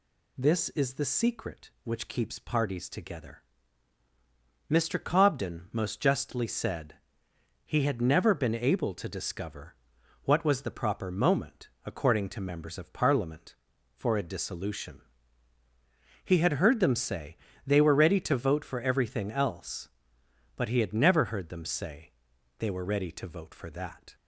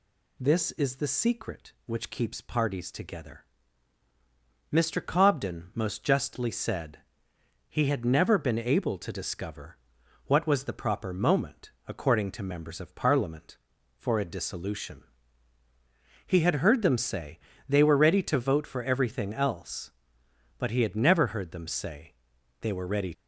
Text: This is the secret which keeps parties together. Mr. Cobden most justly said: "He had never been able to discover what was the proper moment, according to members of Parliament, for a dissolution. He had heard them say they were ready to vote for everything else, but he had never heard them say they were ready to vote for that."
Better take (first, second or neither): first